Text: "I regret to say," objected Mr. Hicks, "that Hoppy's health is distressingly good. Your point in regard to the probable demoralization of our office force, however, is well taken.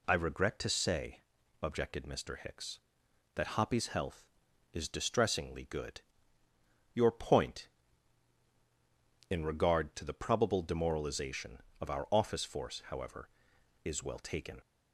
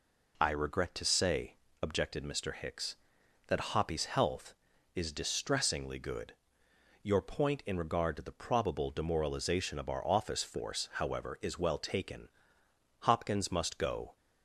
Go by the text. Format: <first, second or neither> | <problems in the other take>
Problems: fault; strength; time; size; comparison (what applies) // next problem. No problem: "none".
first | goes on to say "Hopkins must go"; noticeable; from 13.0 s on; 1.1 s long